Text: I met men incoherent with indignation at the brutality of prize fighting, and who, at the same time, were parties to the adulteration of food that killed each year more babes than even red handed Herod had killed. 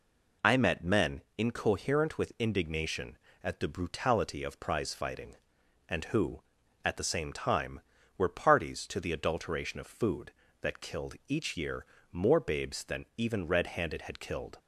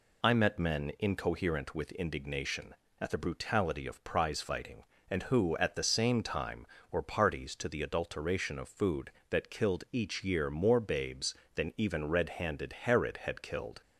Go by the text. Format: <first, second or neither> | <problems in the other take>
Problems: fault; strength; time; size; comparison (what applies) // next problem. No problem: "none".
second | pauses between "men" and "incoherent"; slight; at 1.2 s; 0.16 s long // pauses between "year" and "more"; slight; at 11.8 s; 0.26 s long // skips "Herod"; at 14.0 s